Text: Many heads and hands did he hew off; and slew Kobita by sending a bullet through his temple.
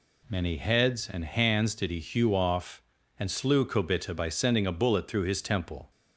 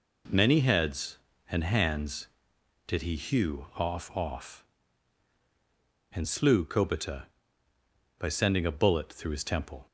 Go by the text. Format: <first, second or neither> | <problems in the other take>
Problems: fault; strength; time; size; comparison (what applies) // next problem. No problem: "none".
first | says "off" twice; at 4.1 s